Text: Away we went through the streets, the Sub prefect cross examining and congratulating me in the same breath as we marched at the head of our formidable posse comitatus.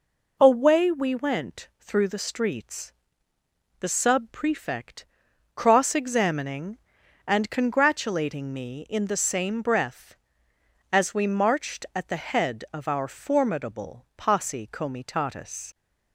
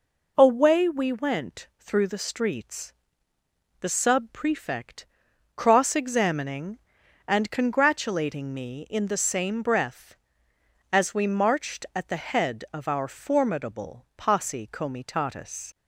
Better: neither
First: pauses between "prefect" and "cross"; noticeable; at 5.0 s; 0.50 s long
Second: pauses between "prefect" and "cross"; noticeable; at 5.0 s; 0.50 s long

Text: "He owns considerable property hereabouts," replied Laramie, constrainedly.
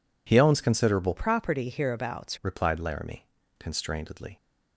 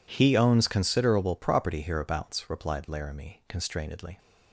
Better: second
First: changes voice from "property" to "hereabouts"; from 1.1 to 2.3 s; 1.2 s long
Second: none

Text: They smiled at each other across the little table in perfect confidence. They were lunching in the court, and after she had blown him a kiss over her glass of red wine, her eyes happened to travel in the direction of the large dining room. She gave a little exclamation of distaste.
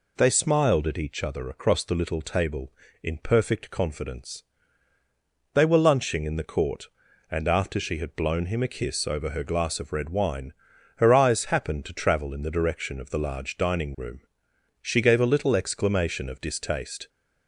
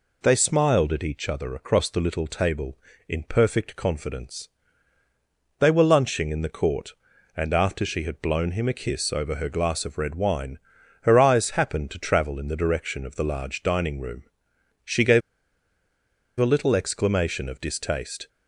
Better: first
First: none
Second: pauses between "gave" and "a"; at 15.2 s; 1.1 s long

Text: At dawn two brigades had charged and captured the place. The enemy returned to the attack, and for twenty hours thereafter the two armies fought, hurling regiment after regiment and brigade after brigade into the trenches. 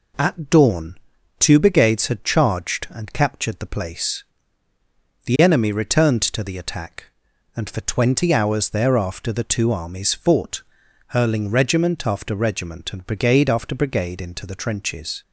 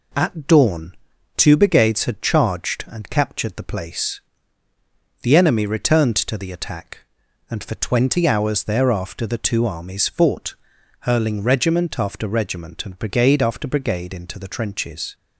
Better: neither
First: pauses between "dawn" and "two"; at 0.9 s; 0.42 s long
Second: pauses between "dawn" and "two"; at 0.9 s; 0.42 s long

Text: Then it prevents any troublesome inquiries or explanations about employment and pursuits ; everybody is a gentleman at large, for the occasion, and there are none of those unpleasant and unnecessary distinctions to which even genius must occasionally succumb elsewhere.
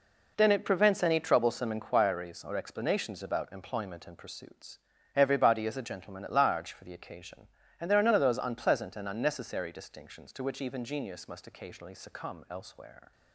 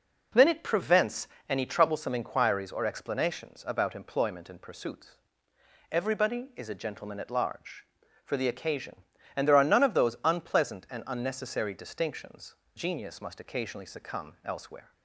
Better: first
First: none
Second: pauses between "prevents" and "any"; slight; at 1.2 s; 0.20 s long // skips "to which even"; at 12.6 s

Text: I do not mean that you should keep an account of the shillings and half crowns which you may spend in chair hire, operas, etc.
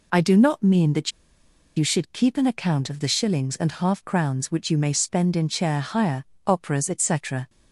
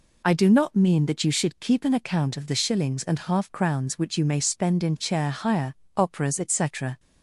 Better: second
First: pauses between "that" and "you"; noticeable; at 1.1 s; 0.66 s long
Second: none

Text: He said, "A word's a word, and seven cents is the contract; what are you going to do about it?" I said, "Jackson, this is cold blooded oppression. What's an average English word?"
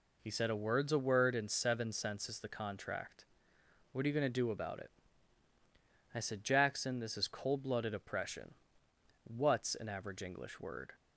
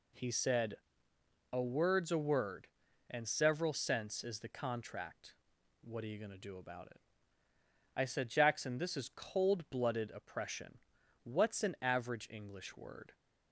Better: first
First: none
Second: says "several" for "seven"; at 3.2 s

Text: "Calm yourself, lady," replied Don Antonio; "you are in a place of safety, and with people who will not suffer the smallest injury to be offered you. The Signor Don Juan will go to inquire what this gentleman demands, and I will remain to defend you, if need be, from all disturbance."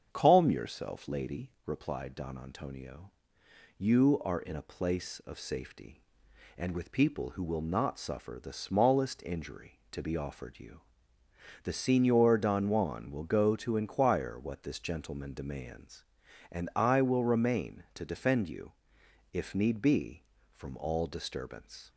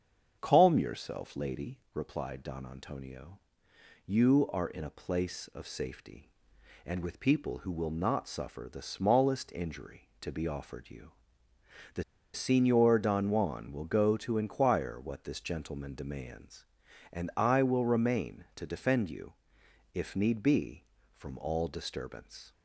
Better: first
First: starts louder than the rest; strong; until 1.1 s; 7.5 dB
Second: starts louder than the rest; strong; until 1.4 s; 7.5 dB // pauses between "The" and "Signor"; slight; at 12.0 s; 0.31 s long

